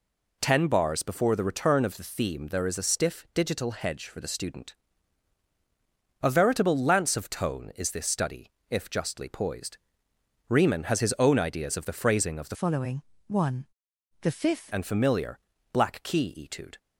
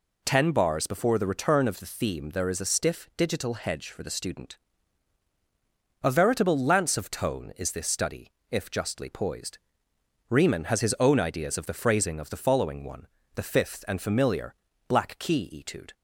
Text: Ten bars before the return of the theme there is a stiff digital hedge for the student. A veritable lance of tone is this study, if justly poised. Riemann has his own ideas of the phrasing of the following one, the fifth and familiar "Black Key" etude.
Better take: second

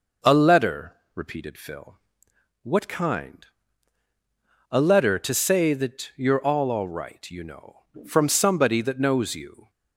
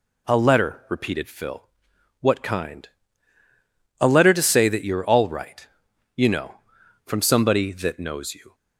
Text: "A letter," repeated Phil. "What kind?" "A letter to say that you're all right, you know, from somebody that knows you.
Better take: second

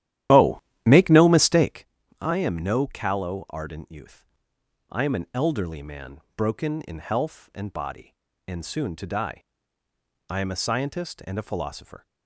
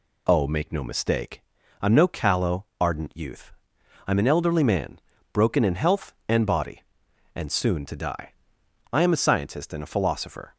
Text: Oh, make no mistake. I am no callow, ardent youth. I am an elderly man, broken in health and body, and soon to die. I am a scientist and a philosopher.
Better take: second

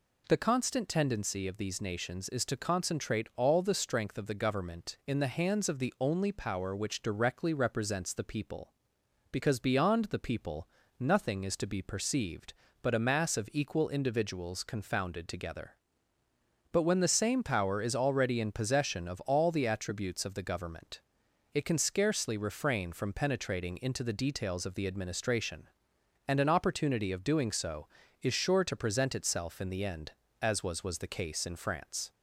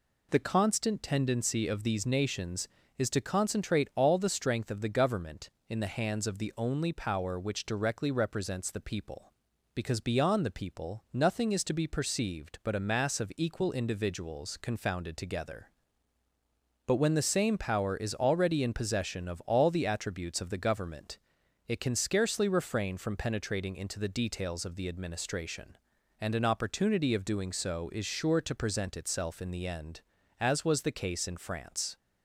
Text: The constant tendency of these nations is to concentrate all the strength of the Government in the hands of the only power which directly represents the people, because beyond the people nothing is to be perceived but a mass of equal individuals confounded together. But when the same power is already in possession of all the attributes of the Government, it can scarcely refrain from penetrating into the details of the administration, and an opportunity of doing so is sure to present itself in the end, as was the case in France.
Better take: second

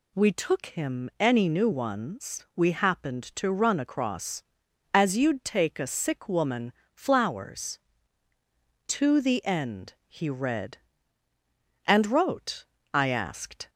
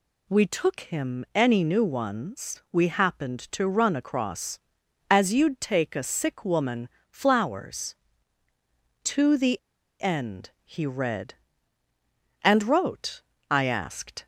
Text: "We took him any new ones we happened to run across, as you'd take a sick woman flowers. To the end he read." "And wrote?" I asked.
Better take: first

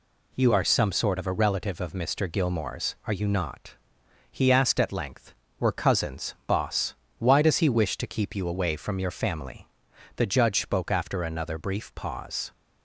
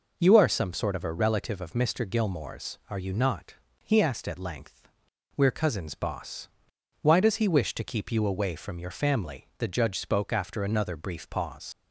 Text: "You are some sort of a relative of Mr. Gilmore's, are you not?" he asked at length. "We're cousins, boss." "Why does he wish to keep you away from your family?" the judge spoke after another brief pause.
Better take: first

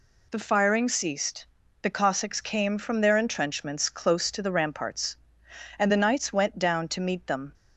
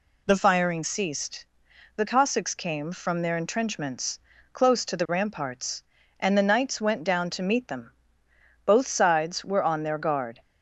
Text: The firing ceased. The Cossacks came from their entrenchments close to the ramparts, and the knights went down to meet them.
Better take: first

